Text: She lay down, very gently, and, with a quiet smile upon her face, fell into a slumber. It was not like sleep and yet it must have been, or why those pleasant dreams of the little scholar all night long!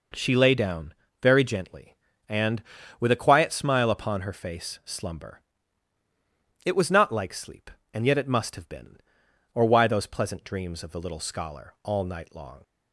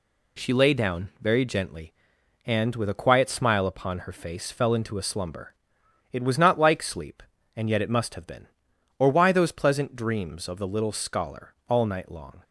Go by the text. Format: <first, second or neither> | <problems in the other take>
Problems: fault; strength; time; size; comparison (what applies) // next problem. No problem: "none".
second | skips "fell into a"; at 4.8 s